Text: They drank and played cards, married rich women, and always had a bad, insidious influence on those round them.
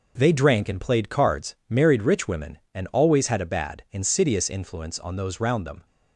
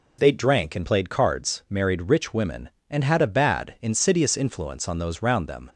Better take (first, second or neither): first